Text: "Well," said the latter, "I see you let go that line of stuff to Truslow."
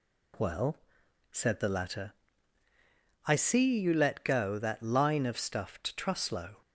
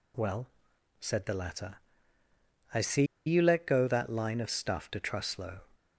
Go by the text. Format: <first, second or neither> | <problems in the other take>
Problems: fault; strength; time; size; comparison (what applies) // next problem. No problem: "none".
first | pauses between "see" and "you"; slight; at 3.0 s; 0.22 s long